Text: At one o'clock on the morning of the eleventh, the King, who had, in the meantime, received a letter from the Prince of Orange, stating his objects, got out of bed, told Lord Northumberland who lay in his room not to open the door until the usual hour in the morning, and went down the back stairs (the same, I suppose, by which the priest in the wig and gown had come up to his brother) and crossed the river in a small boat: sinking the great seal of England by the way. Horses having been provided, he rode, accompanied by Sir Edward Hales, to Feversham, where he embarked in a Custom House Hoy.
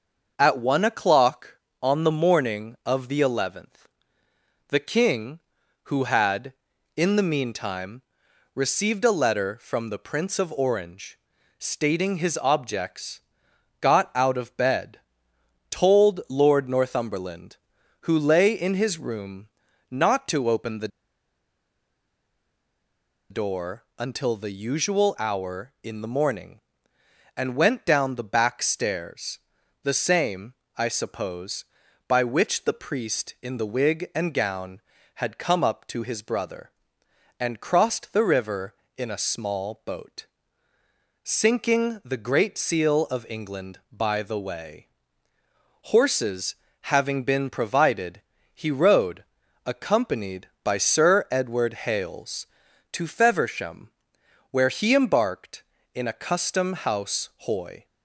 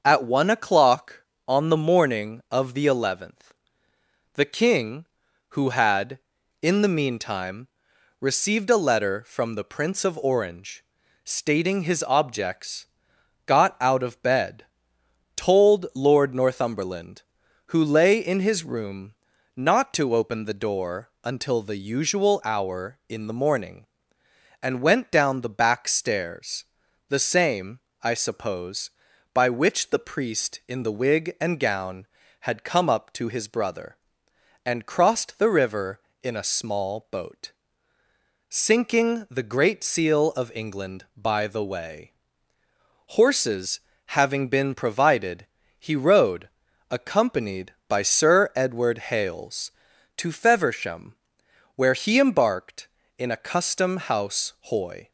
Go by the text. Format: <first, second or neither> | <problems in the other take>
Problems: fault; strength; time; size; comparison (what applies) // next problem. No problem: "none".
second | starts louder than the rest; until 1.3 s; 6.5 dB; also in the second // pauses between "room" and "not"; at 19.4 s; 0.44 s long; also in the second // pauses between "the" and "door"; strong; at 20.8 s; 2.4 s long // pauses between "door" and "until"; slight; at 23.8 s; 0.16 s long; slight in the second // pauses between "Horses" and "having"; slight; at 46.5 s; 0.30 s long; slight in the second